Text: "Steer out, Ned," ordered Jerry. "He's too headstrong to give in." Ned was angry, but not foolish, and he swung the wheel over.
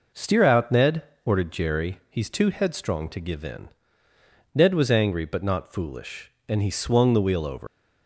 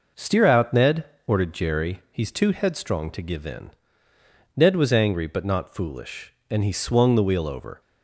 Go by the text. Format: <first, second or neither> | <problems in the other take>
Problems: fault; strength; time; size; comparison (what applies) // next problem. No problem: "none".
second | leaves "over" unfinished; at 7.6 s; 115 ms